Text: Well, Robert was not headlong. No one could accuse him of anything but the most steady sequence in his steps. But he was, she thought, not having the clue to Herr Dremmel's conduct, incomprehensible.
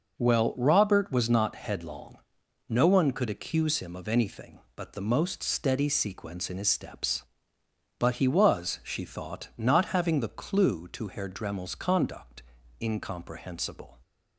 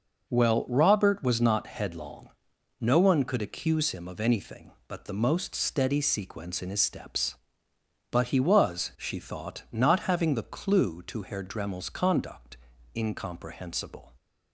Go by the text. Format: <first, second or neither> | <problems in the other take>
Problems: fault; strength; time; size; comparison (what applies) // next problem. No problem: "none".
neither | none